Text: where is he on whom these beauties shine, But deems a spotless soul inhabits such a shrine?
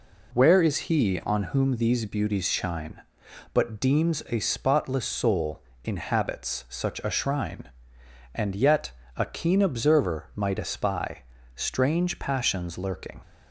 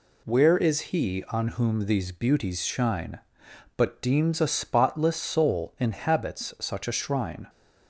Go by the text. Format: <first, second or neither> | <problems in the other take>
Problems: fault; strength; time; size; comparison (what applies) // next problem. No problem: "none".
second | pauses between "soul" and "inhabits"; slight; at 5.6 s; 0.22 s long // goes on to say "And yet a keen observer might espy Strange passions lurking"; strong; from 8.3 s on; 4.8 s long